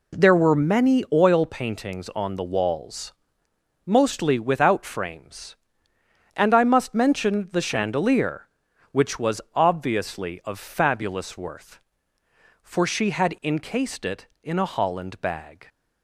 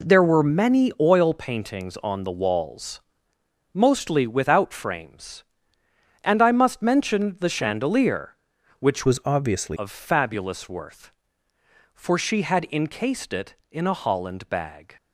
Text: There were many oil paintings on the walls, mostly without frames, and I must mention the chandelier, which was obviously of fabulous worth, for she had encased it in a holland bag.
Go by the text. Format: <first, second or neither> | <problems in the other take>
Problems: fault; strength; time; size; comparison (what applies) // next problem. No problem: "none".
first | changes voice from "was" to "obviously"; from 9.0 to 9.7 s; 0.7 s long